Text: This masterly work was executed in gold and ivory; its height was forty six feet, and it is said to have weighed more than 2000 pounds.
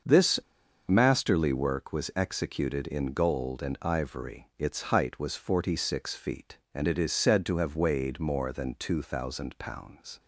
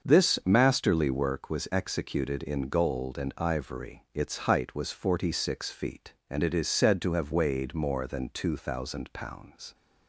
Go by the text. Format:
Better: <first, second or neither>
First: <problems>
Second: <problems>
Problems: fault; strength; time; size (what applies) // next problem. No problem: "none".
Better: second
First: starts louder than the rest; until 1.5 s; 6.5 dB // pauses between "This" and "masterly"; noticeable; at 0.3 s; 0.50 s long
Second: starts louder than the rest; until 1.1 s; 6.5 dB